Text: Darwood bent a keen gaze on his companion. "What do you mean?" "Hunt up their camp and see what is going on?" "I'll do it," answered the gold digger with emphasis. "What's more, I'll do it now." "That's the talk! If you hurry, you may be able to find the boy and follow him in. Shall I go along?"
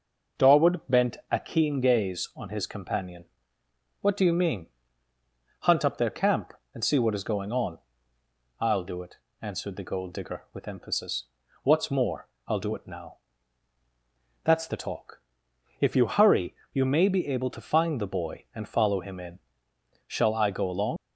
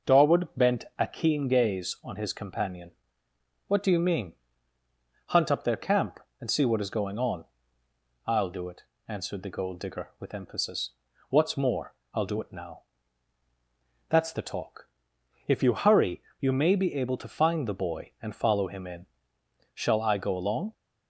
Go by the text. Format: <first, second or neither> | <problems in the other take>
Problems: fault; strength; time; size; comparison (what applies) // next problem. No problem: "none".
second | leaves "along" unfinished; at 20.9 s; 95 ms